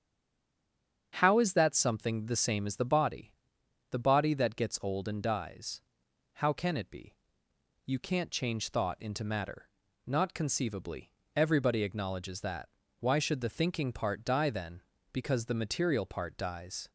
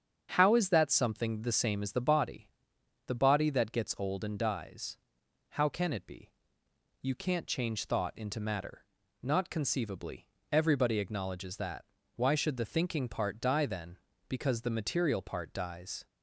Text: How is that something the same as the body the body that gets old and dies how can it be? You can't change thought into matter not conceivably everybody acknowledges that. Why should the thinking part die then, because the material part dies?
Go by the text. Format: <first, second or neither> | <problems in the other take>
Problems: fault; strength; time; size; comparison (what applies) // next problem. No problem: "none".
second | stays silent before the first word; until 1.1 s; 1.1 s long // starts louder than the rest; strong; until 2.1 s; 7.5 dB; strong in the second // pauses between "body" and "the"; noticeable; at 3.3 s; 0.58 s long; noticeable in the second // pauses between "dies" and "how"; noticeable; at 5.7 s; 0.54 s long; noticeable in the second // pauses between "matter" and "not"; at 9.6 s; 0.40 s long; also in the second // pauses between "conceivably" and "everybody"; slight; at 11.1 s; 0.24 s long; slight in the second